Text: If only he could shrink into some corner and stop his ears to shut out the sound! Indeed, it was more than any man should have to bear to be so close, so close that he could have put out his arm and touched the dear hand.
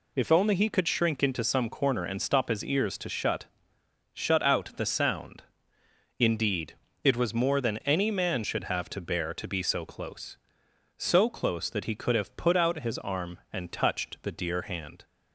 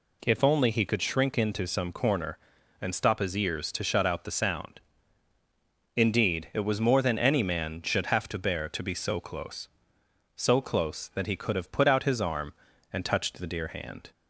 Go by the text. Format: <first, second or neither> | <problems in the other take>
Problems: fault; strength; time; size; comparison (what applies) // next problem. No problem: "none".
second | says "shut" twice; at 4.1 s